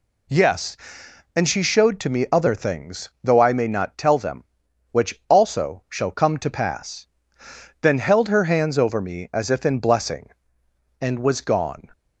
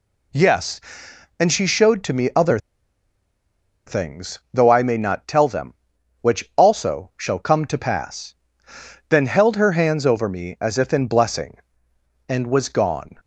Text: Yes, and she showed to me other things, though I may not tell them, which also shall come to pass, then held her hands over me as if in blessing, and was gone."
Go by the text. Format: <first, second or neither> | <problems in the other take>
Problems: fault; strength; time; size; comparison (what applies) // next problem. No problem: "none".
first | pauses between "other" and "things"; strong; at 2.5 s; 1.2 s long